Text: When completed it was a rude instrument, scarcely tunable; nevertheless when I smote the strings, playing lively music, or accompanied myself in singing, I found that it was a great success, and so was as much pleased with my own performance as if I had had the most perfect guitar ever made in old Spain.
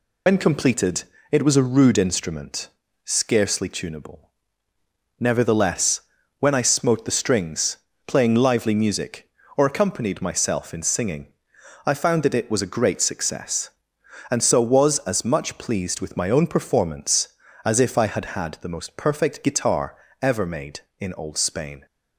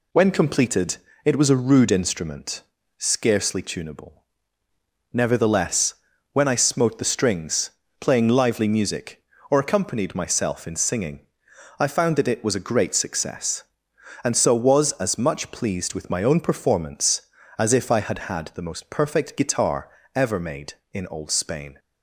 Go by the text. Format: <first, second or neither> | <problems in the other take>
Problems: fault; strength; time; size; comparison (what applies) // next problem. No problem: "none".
second | loses the start of "When"; at 0.2 s; 70 ms // pauses between "completed" and "it"; slight; at 1.0 s; 0.28 s long; slight in the second // pauses between "nevertheless" and "when"; at 5.9 s; 0.40 s long; also in the second // pauses between "guitar" and "ever"; slight; at 19.9 s; 0.24 s long; slight in the second